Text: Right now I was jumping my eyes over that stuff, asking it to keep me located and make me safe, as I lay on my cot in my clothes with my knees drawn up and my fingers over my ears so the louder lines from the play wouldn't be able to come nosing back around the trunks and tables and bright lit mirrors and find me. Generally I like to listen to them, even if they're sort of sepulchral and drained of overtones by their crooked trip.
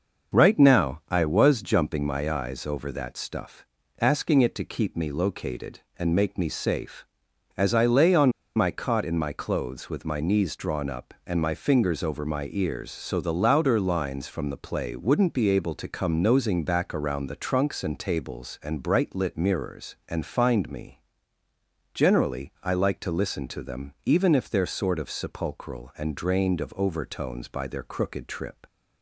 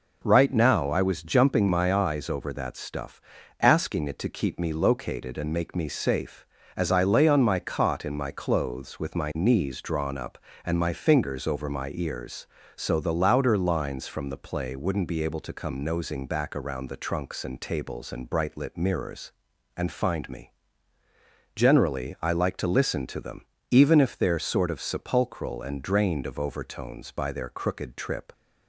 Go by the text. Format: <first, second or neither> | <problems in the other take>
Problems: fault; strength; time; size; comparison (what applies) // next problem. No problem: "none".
second | pauses between "on" and "my"; slight; at 8.3 s; 0.25 s long